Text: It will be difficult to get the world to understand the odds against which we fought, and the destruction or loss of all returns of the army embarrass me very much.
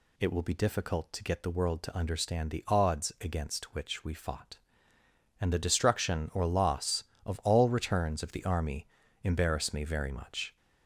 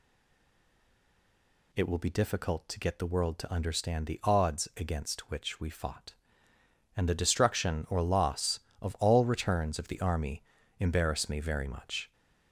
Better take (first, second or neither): first